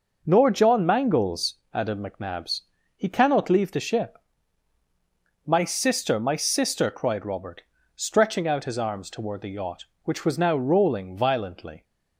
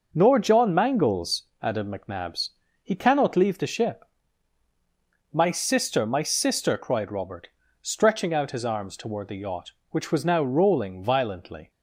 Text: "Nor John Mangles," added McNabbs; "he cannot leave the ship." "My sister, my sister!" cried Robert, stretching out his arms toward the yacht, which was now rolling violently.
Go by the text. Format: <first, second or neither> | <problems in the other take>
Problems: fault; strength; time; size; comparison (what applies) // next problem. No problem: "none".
neither | none